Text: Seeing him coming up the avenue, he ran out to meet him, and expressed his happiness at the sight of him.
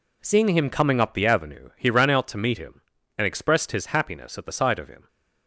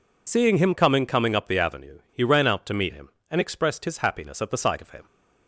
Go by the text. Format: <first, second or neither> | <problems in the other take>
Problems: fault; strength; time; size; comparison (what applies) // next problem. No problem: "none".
first | says "coming" twice; at 1.0 s